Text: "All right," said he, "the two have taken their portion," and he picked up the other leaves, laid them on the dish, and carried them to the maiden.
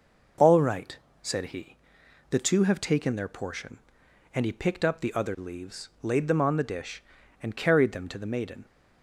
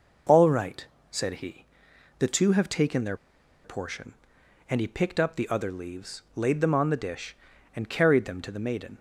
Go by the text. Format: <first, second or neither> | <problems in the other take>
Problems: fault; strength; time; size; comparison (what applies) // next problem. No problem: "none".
first | pauses between "their" and "portion"; noticeable; at 3.1 s; 0.48 s long